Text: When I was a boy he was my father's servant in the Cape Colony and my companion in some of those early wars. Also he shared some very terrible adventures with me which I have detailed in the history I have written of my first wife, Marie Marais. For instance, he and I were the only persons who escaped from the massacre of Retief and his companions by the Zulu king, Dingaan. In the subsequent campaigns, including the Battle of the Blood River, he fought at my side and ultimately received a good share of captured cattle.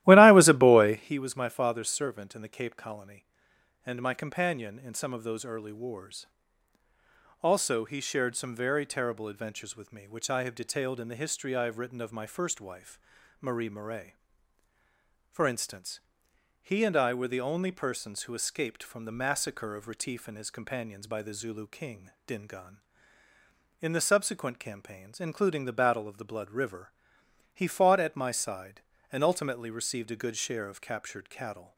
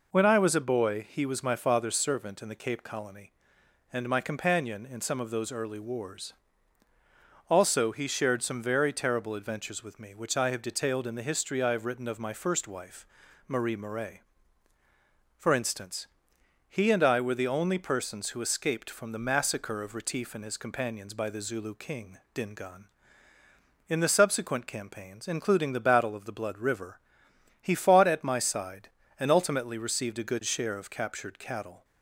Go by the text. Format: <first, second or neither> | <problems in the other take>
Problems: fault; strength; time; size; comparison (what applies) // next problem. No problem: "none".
second | starts louder than the rest; strong; until 1.2 s; 16 dB